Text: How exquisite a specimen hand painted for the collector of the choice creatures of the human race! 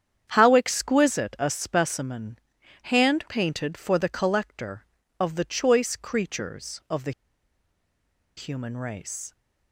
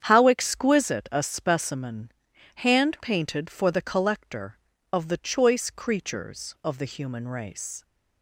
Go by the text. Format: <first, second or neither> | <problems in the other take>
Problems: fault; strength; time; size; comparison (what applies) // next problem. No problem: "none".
second | starts louder than the rest; strong; until 1.3 s; 8.5 dB; strong in the second // pauses between "specimen" and "hand"; at 2.3 s; 0.44 s long; also in the second // pauses between "the" and "human"; strong; at 7.1 s; 1.2 s long